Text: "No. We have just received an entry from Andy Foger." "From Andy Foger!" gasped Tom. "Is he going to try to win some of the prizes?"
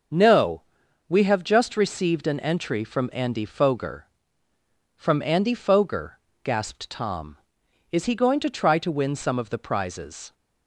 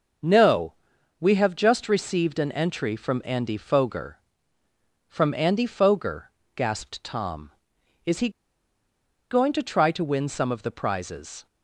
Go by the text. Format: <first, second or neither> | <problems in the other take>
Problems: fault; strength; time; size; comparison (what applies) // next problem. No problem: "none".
first | starts louder than the rest; until 1.7 s; 6 dB; also in the first // pauses between "he" and "going"; at 8.2 s; 1.0 s long